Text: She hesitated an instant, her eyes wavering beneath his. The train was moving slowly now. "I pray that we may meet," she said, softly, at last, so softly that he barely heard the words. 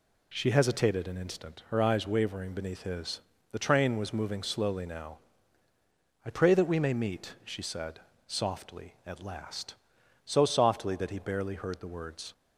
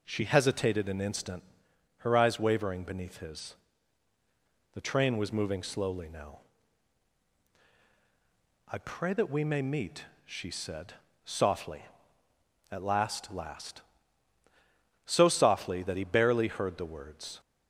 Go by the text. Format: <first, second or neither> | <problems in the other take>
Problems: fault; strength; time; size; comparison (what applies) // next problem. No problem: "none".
first | says "last" twice; at 13.3 s